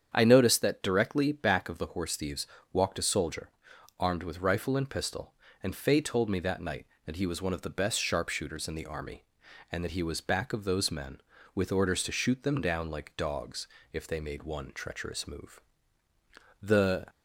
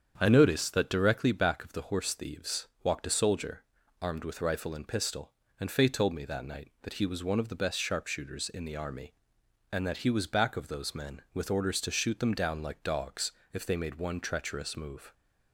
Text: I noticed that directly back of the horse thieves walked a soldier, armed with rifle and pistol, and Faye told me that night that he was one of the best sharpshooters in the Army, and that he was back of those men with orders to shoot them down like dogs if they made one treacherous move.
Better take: second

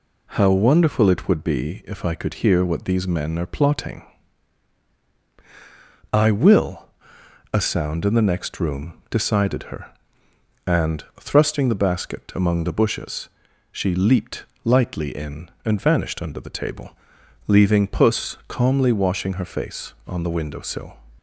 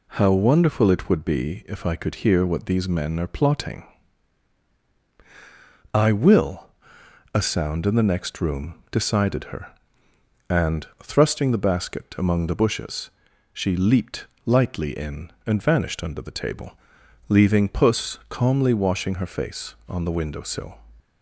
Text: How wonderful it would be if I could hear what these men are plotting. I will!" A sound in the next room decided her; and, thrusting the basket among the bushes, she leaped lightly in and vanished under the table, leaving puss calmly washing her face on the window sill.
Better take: neither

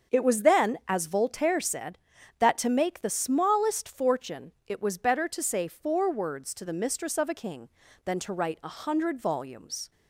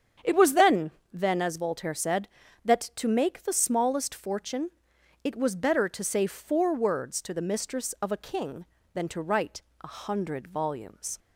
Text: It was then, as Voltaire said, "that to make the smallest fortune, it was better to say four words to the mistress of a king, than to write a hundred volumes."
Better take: first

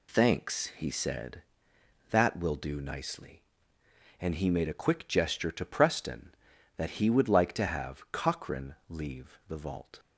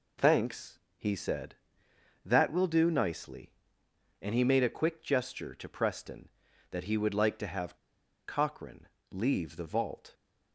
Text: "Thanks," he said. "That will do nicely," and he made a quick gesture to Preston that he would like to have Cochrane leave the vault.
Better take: first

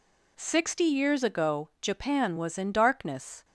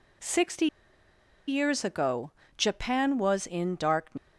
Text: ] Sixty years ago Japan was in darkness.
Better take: first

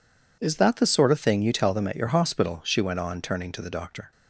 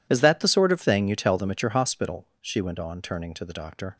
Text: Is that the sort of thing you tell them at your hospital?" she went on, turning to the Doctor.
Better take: neither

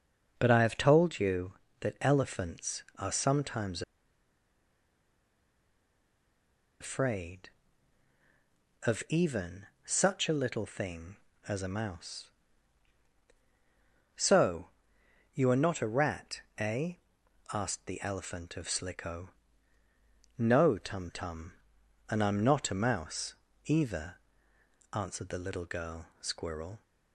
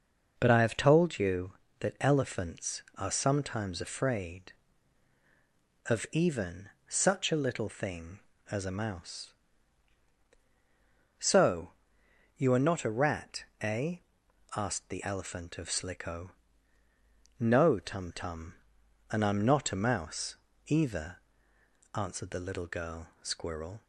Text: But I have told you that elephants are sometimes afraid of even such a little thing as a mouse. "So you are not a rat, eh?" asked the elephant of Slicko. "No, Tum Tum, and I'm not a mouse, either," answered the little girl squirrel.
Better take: second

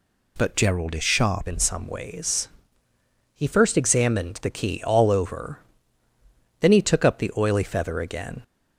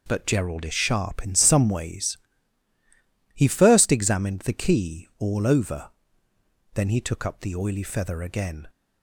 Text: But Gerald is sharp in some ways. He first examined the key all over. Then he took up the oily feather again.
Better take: second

